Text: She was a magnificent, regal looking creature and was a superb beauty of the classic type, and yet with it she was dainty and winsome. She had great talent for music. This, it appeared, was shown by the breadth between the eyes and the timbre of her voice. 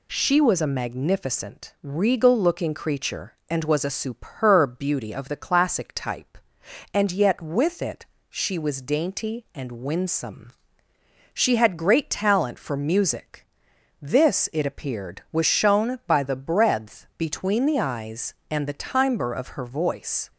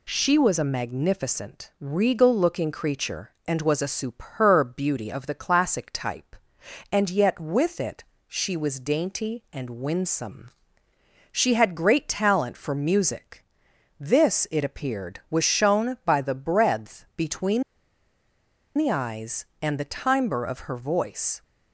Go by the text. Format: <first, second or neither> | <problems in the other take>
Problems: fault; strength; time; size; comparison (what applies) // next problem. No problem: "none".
first | pauses between "it" and "she"; slight; at 8.0 s; 0.22 s long; slight in the first // pauses between "between" and "the"; at 17.6 s; 1.1 s long